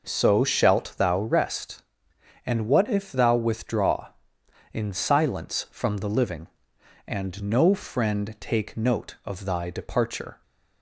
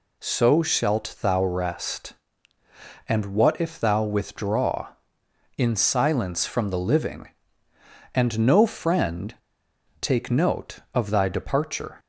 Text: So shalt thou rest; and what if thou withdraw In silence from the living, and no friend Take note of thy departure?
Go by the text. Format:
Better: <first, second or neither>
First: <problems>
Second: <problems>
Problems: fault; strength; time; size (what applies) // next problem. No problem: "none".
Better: first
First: none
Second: pauses between "friend" and "Take"; noticeable; at 9.3 s; 0.64 s long